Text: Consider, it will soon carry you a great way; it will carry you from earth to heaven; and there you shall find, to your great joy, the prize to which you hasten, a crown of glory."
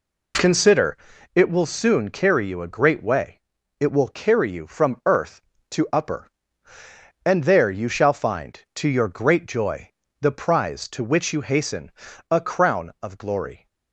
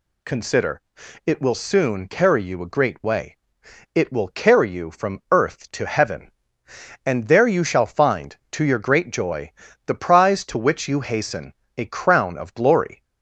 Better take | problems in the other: second | says "upper" for "heaven"; at 5.9 s

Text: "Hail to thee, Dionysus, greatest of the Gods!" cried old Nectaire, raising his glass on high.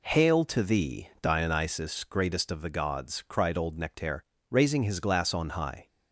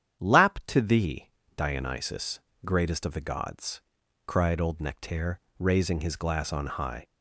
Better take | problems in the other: first | starts louder than the rest; strong; until 1.2 s; 9 dB // says "Lap" for "Hail"; at 0.2 s

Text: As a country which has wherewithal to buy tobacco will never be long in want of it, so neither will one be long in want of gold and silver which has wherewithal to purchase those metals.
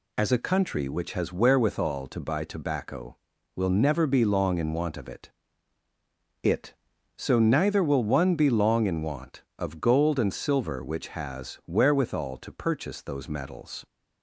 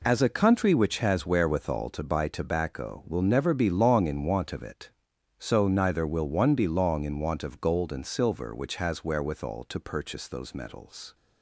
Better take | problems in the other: second | says "it" twice; at 6.4 s

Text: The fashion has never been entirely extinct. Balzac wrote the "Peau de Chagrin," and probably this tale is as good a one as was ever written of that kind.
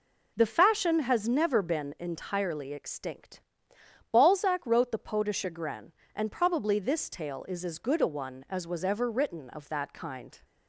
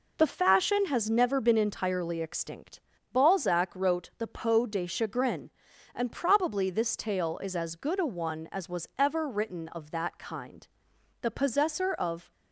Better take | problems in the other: first | goes on to say "The possessor of"; noticeable; from 11.2 s on; 1.1 s long

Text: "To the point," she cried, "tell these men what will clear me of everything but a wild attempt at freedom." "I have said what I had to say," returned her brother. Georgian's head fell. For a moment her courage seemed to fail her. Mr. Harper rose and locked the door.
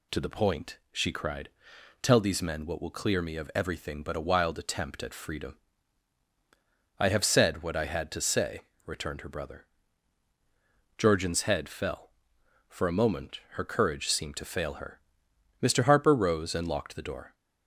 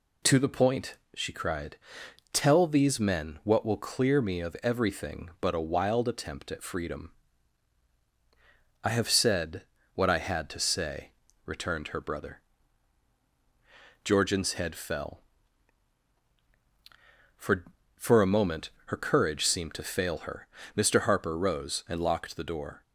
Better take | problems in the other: first | pauses between "said" and "what"; slight; at 9.6 s; 0.30 s long // says "For" twice; at 17.9 s // pauses between "moment" and "her"; slight; at 18.7 s; 0.16 s long

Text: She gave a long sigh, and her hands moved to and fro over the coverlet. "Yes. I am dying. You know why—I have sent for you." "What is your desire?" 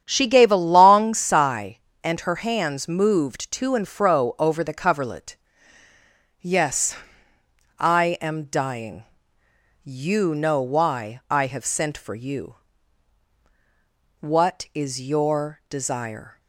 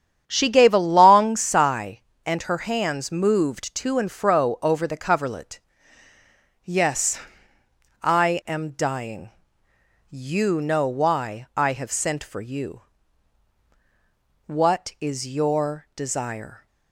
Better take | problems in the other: neither | starts louder than the rest; strong; the same in both

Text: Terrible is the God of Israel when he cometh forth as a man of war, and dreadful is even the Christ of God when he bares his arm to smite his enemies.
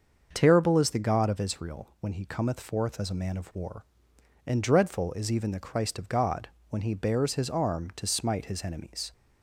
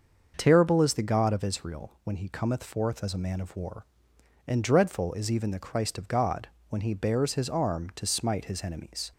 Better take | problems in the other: neither | starts louder than the rest; the same in both // pauses between "God" and "when"; slight; the same in both

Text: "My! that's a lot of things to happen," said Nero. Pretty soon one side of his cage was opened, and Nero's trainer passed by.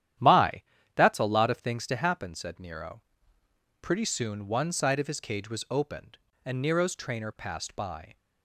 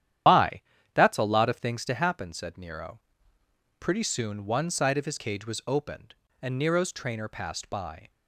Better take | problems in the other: first | loses the start of "My"; at 0.2 s; 80 ms // starts louder than the rest; strong; until 1.5 s; 10.5 dB; strong in the first

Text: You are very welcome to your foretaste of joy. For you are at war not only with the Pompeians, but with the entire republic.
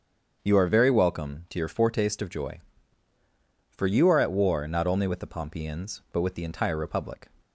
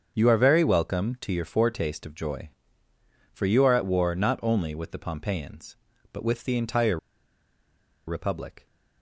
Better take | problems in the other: first | starts louder than the rest; until 1.1 s; 7 dB; strong in the first // pauses between "entire" and "republic"; at 6.9 s; 1.0 s long

